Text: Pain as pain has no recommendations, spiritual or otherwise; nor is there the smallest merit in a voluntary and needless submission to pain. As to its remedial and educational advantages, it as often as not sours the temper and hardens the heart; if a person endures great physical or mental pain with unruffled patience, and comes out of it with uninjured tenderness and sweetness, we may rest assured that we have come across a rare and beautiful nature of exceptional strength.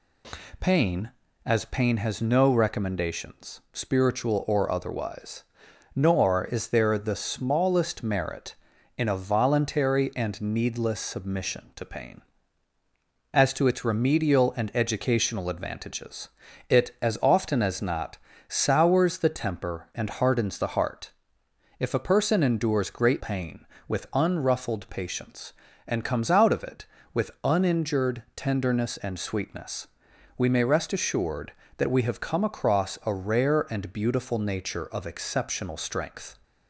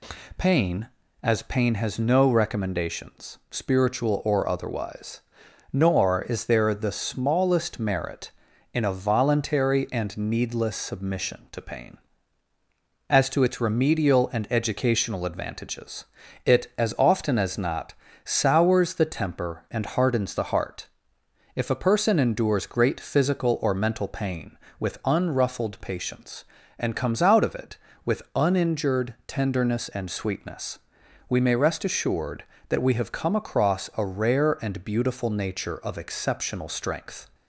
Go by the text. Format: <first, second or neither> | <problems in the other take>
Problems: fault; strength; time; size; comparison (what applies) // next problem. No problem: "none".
second | pauses between "not" and "sours"; slight; at 18.1 s; 0.30 s long; slight in the second // skips "physical or mental"; at 23.2 s